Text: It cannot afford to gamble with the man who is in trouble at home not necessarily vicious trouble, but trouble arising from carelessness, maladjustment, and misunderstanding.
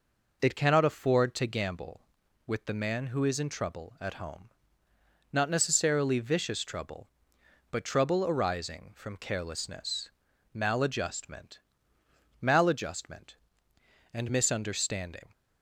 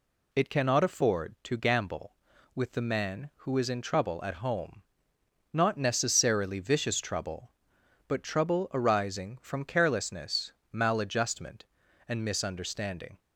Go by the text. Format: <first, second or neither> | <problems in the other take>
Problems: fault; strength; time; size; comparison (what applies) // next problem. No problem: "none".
second | pauses between "home" and "not"; noticeable; at 4.4 s; 0.82 s long; noticeable in the second // says "maladjustment" twice; at 12.4 s